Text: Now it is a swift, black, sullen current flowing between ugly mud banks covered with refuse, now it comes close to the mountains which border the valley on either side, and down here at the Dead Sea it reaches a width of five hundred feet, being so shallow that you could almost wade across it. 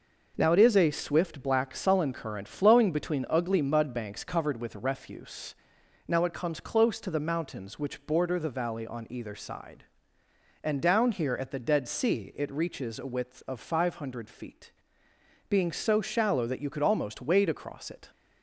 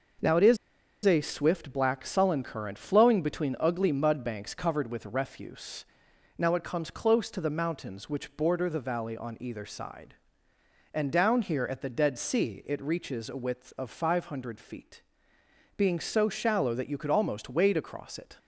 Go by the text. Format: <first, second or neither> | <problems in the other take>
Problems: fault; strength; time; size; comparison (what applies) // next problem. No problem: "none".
first | pauses between "is" and "a"; noticeable; at 0.5 s; 0.48 s long